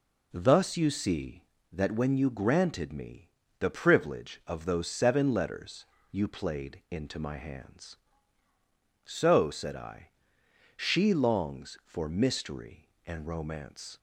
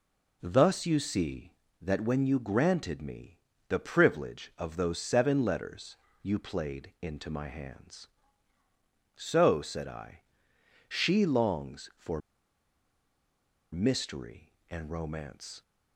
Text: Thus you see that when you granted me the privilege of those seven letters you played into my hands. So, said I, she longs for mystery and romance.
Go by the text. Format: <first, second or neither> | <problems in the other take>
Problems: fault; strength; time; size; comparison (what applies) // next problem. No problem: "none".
first | pauses between "me" and "the"; slight; at 3.3 s; 0.32 s long; slight in the first // pauses between "letters" and "you"; slight; at 5.9 s; 0.26 s long; slight in the first // pauses between "for" and "mystery"; strong; at 12.1 s; 1.5 s long